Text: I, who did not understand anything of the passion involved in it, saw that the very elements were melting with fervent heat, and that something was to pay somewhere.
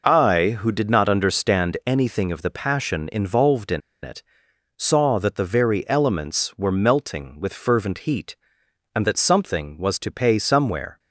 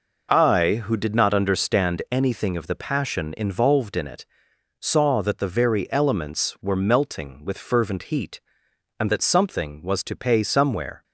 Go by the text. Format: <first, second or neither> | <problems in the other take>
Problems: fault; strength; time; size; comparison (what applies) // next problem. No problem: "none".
second | pauses between "in" and "it"; slight; at 3.8 s; 0.22 s long